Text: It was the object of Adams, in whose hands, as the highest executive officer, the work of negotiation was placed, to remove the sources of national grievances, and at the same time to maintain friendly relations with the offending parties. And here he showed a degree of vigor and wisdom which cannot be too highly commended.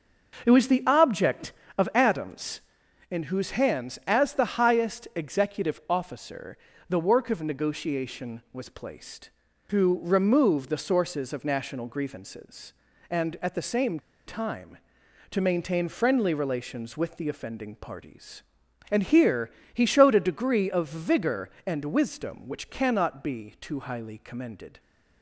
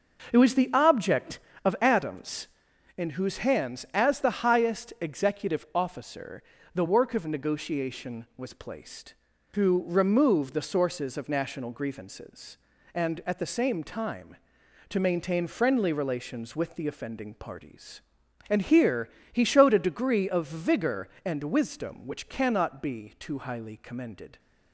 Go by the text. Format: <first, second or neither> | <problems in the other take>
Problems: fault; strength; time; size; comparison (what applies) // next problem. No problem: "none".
second | starts louder than the rest; noticeable; until 1.4 s; 6 dB; noticeable in the second // pauses between "same" and "time"; slight; at 13.9 s; 0.28 s long // pauses between "here" and "he"; slight; at 19.5 s; 0.20 s long; slight in the second